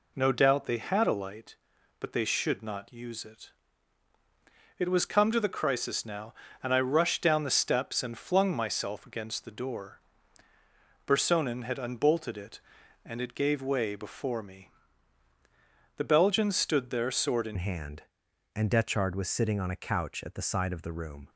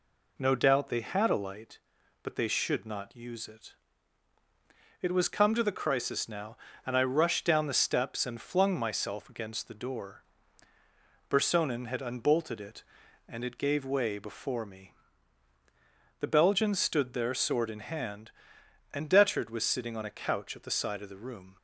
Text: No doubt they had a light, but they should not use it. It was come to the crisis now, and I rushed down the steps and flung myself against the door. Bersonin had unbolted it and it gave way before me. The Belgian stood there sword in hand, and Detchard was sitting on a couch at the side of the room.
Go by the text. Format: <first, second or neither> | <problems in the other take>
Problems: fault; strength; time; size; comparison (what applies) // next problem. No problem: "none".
second | changes voice at "hand"; from 17.5 s on; 3.7 s long